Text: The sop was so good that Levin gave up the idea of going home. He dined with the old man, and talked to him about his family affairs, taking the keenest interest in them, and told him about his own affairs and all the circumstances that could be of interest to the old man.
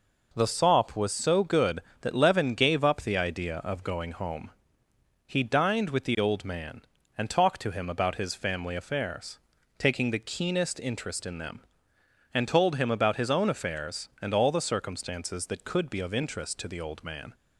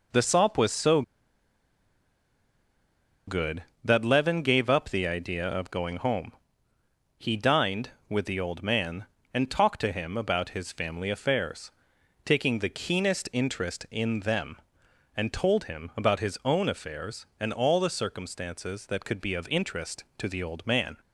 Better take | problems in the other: first | pauses between "so" and "good"; strong; at 1.0 s; 2.2 s long

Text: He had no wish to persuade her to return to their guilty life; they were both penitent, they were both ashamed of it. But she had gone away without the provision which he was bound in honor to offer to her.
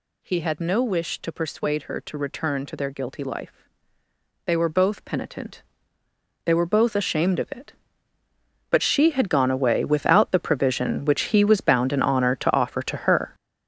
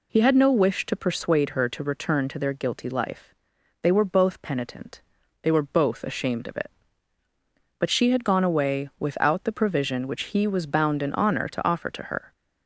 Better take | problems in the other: second | gets louder; strong; throughout; 9.5 dB

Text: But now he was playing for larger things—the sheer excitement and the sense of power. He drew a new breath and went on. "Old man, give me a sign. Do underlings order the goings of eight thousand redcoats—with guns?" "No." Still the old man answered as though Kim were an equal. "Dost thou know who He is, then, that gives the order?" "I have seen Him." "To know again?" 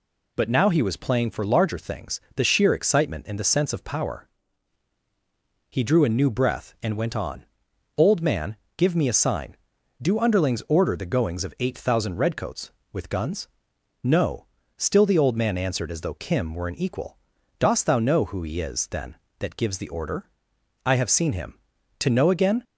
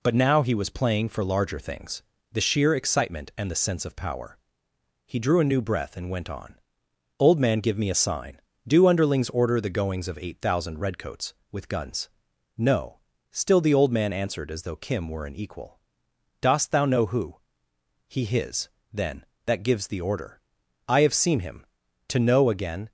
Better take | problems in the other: first | pauses between "who" and "He"; noticeable; at 17.3 s; 0.72 s long // says "his" for "is"; at 18.2 s

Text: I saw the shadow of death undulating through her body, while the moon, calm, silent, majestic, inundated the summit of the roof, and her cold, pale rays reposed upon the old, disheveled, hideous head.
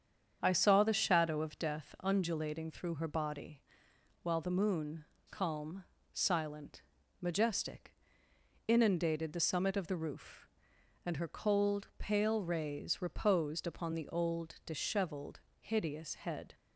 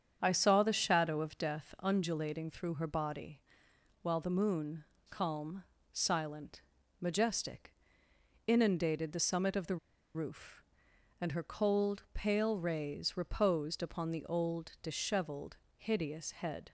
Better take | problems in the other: first | starts louder than the rest; strong; until 1.2 s; 7.5 dB; strong in the first // pauses between "the" and "roof"; at 9.7 s; 0.37 s long

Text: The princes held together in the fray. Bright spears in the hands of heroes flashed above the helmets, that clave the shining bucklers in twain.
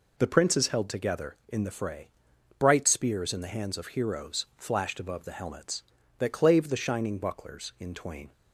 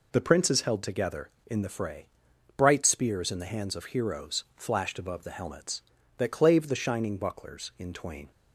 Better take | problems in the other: neither | none

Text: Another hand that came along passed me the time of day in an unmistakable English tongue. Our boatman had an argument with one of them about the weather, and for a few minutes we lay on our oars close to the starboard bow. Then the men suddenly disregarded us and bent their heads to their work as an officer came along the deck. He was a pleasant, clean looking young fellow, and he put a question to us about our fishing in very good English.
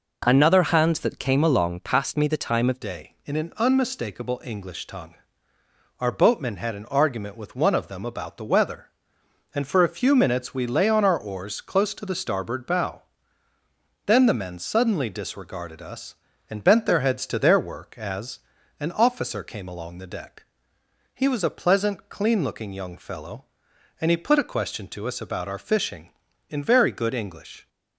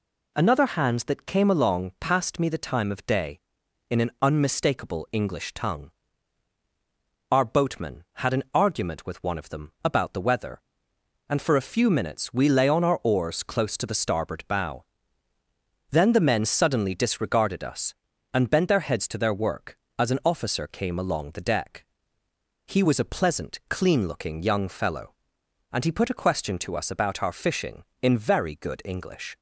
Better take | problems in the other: second | changes voice at "day"; from 2.8 s on; 24.8 s long // pauses between "as" and "an"; at 18.4 s; 0.38 s long

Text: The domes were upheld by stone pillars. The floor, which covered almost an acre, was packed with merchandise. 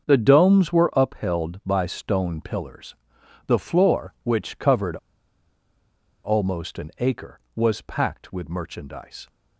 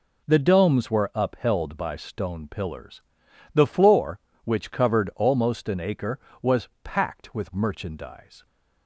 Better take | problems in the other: second | starts louder than the rest; until 1.1 s; 6.5 dB // pauses between "covered" and "almost"; strong; at 4.9 s; 1.2 s long

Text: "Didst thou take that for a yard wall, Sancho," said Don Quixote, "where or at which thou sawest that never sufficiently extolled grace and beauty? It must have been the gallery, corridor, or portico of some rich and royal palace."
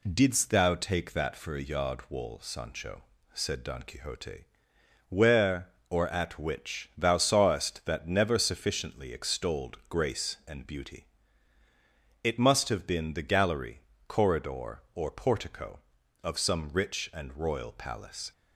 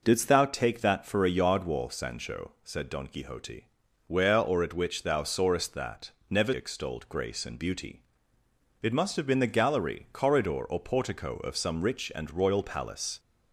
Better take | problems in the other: first | pauses between "that" and "never"; slight; at 6.1 s; 0.18 s long // skips "sufficiently"; at 6.5 s

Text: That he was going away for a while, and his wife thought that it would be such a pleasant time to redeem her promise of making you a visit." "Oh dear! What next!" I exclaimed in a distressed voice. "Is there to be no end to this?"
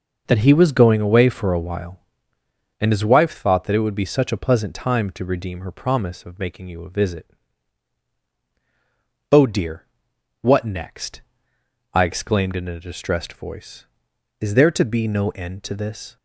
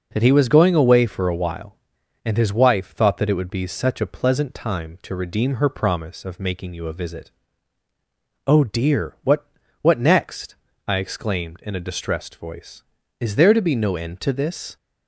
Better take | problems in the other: first | says "What" twice; at 9.7 s

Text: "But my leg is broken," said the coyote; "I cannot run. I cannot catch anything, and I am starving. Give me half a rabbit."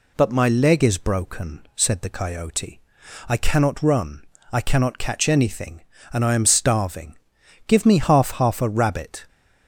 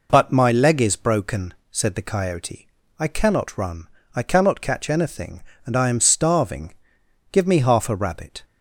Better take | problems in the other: second | says "half" twice; at 8.3 s

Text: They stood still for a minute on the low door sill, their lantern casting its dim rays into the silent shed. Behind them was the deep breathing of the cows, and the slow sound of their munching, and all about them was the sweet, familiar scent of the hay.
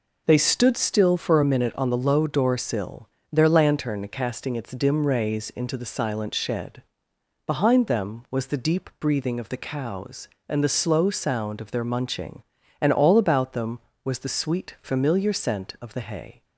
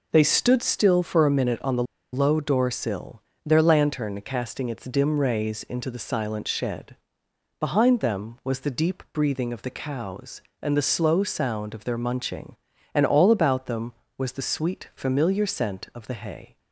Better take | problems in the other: first | pauses between "the" and "low"; slight; at 1.8 s; 0.29 s long

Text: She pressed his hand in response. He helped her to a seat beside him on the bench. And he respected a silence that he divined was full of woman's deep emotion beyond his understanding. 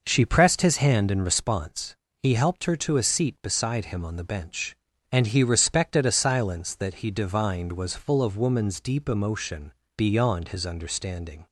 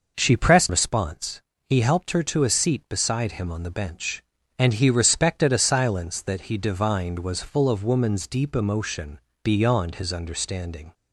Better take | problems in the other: first | skips "his hand in"; at 0.6 s // pauses between "emotion" and "beyond"; slight; at 9.1 s; 0.24 s long; slight in the first

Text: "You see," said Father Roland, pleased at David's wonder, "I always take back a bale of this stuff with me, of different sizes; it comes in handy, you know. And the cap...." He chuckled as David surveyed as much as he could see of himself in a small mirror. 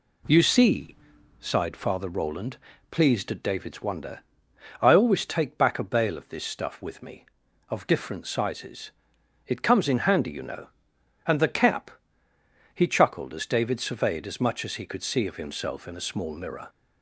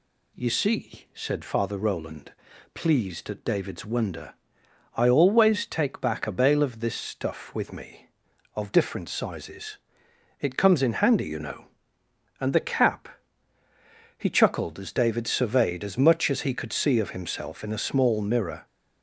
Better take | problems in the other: second | says "sighed" for "said"; at 1.4 s

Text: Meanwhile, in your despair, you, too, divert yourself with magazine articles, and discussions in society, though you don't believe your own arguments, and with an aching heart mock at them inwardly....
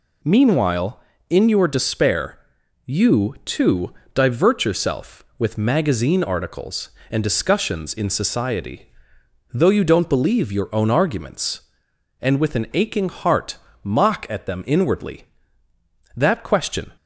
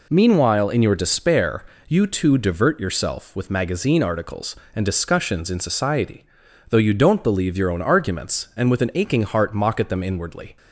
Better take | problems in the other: second | pauses between "heart" and "mock"; slight; at 13.5 s; 0.26 s long // goes on to say "That question"; noticeable; from 16.1 s on; 0.76 s long

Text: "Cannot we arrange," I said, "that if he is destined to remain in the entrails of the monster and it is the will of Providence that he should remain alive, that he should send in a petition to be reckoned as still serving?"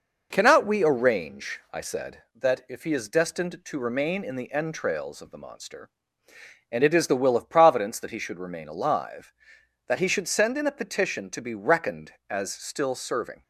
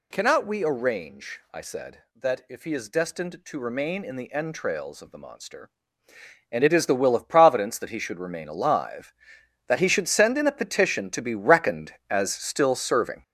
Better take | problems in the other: first | gets louder; strong; throughout; 8 dB

